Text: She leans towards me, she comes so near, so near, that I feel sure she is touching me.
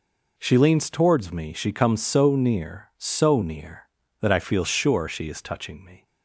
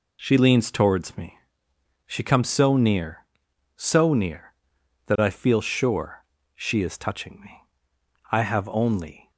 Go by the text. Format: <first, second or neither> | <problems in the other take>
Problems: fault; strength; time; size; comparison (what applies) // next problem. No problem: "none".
first | pauses between "sure" and "she"; slight; at 6.2 s; 0.32 s long // goes on to say "I have only"; noticeable; from 8.3 s on; 1.0 s long